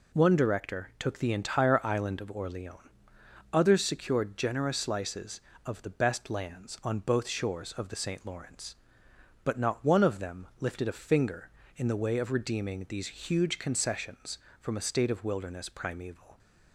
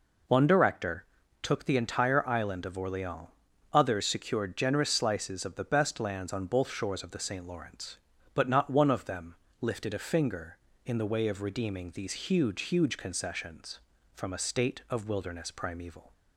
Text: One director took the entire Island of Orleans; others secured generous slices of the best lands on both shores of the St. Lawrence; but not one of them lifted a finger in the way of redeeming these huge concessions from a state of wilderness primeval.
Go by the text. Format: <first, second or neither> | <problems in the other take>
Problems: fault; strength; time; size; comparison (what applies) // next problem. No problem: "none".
first | pauses between "director" and "took"; slight; at 1.0 s; 0.36 s long // pauses between "them" and "lifted"; slight; at 9.3 s; 0.24 s long // says "huge" twice; at 12.6 s